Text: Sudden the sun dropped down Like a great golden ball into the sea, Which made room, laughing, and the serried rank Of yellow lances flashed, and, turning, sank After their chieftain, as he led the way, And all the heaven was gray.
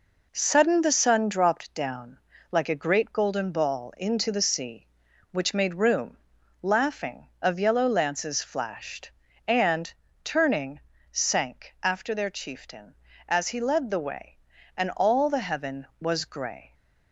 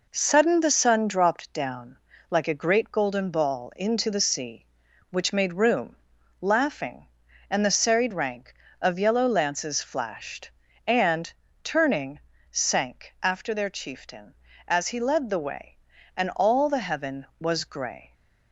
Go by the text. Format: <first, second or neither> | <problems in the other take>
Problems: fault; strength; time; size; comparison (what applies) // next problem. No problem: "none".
second | pauses between "down" and "Like"; slight; at 2.1 s; 0.32 s long; slight in the second // skips "and the serried rank"; at 7.3 s